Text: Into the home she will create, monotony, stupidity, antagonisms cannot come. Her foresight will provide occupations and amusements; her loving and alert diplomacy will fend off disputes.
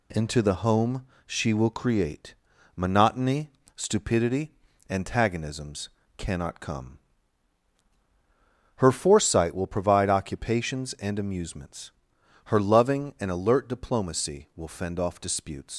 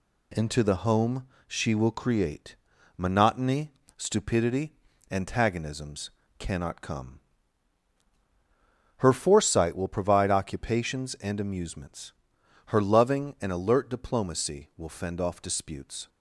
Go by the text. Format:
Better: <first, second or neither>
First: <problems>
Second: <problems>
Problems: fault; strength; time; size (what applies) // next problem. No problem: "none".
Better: second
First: pauses between "home" and "she"; slight; at 1.0 s; 0.20 s long // pauses between "antagonisms" and "cannot"; slight; at 5.8 s; 0.30 s long // leaves "disputes" unfinished; at 15.7 s; 90 ms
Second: pauses between "home" and "she"; slight; at 1.2 s; 0.20 s long // pauses between "antagonisms" and "cannot"; slight; at 6.0 s; 0.30 s long